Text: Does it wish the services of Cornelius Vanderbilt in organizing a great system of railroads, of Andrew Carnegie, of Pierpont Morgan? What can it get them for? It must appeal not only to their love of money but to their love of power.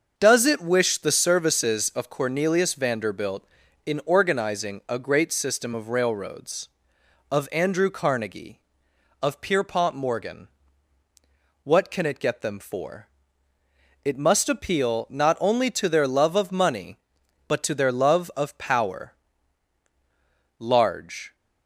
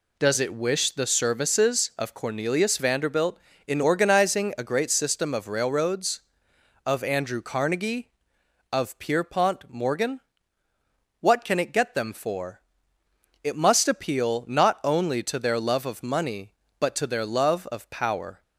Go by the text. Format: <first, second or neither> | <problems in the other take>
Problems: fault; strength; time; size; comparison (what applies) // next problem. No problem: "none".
second | starts louder than the rest; until 1.1 s; 6.5 dB // goes on to say "Large"; noticeable; from 20.6 s on; 0.74 s long